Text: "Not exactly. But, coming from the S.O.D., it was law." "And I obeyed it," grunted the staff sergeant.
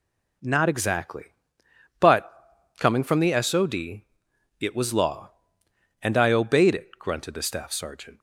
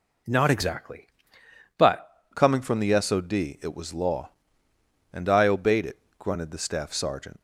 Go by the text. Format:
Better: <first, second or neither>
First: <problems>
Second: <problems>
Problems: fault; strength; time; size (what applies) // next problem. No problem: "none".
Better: first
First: none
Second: changes voice at "coming"; from 2.3 s on; 5.1 s long